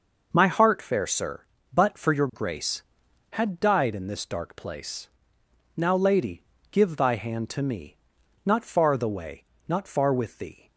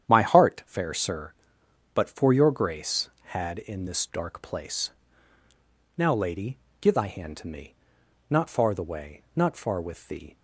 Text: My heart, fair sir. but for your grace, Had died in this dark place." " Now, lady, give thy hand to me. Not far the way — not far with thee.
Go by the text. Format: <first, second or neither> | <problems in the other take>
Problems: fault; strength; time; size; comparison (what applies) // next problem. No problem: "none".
first | starts louder than the rest; strong; until 1.1 s; 9.5 dB // skips "died"; at 3.5 s